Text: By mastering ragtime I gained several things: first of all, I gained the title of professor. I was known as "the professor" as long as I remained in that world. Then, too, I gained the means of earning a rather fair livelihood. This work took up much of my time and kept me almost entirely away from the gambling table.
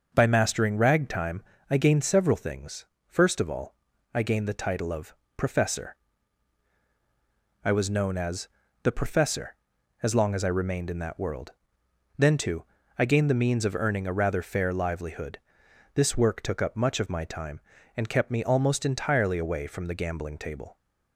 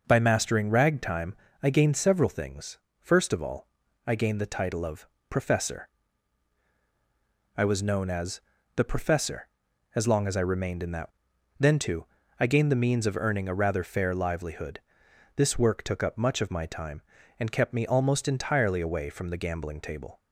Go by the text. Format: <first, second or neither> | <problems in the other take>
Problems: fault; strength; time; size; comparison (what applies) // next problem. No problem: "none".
first | pauses between "ragtime" and "I"; slight; at 1.3 s; 0.28 s long; slight in the first // pauses between "of" and "professor"; slight; at 5.0 s; 0.24 s long; slight in the first // pauses between "as" and "the"; slight; at 8.3 s; 0.36 s long; slight in the first // skips "world"; at 11.3 s